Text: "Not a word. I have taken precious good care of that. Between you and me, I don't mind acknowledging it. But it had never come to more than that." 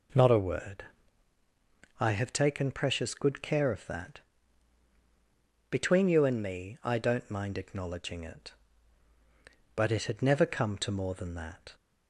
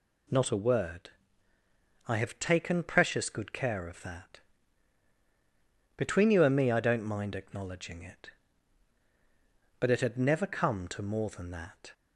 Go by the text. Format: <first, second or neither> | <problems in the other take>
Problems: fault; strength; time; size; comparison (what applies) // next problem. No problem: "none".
neither | none